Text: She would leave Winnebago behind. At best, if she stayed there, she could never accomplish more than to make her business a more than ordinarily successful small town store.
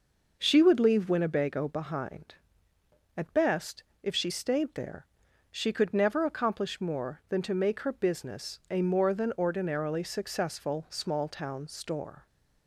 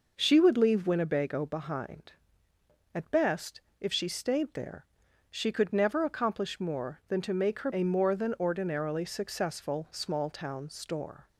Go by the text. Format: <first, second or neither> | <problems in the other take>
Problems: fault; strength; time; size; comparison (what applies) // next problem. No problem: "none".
first | skips "business"; at 7.7 s